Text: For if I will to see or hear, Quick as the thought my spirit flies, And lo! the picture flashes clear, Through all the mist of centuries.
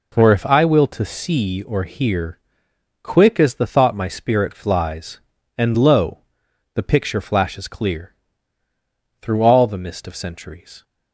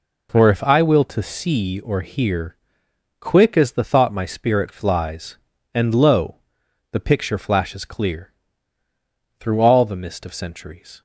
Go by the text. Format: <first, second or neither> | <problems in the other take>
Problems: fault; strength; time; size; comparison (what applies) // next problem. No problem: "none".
neither | none